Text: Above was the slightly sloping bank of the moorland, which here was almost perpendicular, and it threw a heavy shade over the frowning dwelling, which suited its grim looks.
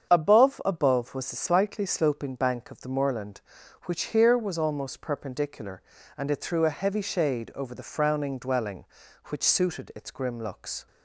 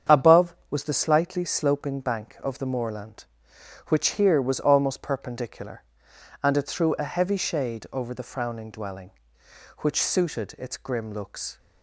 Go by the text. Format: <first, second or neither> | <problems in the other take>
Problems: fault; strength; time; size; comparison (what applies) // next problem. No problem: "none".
second | starts louder than the rest; strong; until 1.1 s; 7.5 dB; strong in the second // says "Above" twice; at 0.6 s